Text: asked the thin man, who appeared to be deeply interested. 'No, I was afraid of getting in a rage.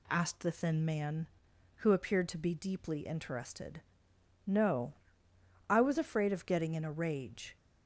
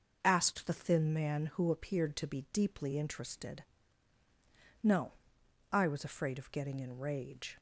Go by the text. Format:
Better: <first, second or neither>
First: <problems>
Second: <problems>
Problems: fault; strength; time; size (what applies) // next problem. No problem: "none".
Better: first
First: none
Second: skips "a"; at 6.9 s